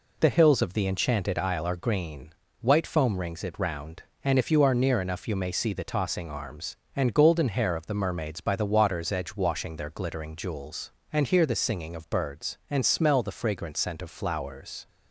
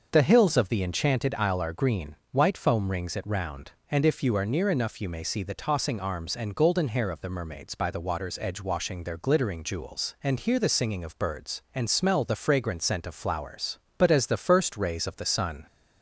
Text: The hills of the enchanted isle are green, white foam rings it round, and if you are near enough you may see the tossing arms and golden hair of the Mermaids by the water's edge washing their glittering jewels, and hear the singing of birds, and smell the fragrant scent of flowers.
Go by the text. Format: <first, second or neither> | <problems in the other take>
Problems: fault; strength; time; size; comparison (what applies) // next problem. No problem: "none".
first | starts louder than the rest; until 1.1 s; 6 dB // goes on to say "But as the first rays of the sun"; strong; from 13.9 s on; 1.6 s long